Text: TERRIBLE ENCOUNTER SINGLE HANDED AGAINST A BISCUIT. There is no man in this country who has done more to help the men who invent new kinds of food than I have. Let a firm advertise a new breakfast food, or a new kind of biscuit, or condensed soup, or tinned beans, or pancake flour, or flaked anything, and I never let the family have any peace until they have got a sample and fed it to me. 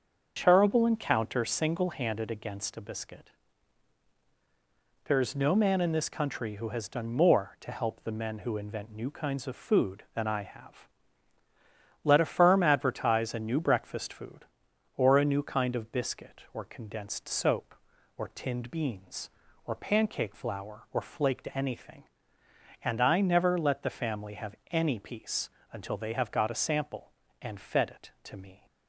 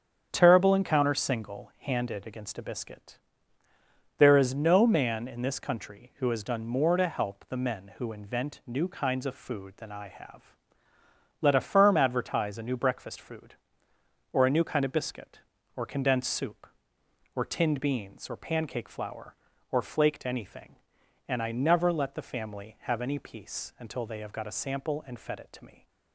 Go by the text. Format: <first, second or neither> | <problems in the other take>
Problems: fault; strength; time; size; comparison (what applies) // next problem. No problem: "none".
second | starts louder than the rest; until 1.3 s; 6.5 dB; strong in the second // says "soap" for "soup"; at 17.2 s // pauses between "have" and "any"; slight; at 24.5 s; 0.16 s long // pauses between "peace" and "until"; slight; at 25.4 s; 0.24 s long